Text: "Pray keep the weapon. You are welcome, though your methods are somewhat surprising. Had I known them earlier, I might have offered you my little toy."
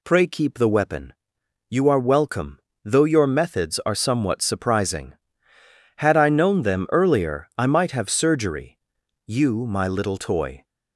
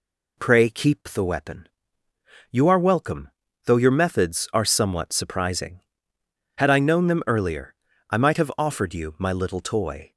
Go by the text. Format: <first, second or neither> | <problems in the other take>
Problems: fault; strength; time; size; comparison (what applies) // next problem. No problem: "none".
second | says "surgery" for "offered"; at 8.0 s